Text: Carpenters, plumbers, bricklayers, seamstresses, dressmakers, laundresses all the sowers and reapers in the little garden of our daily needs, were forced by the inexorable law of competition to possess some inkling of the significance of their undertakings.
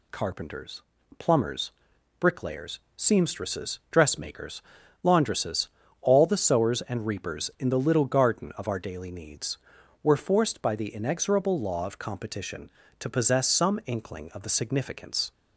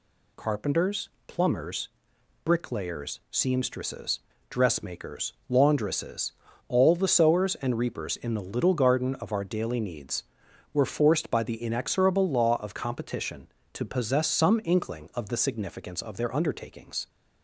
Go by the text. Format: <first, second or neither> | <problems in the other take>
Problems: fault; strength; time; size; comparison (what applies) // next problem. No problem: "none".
second | pauses between "laundresses" and "all"; slight; at 5.6 s; 0.32 s long; slight in the second // stops before "of their undertakings"; at 15.3 s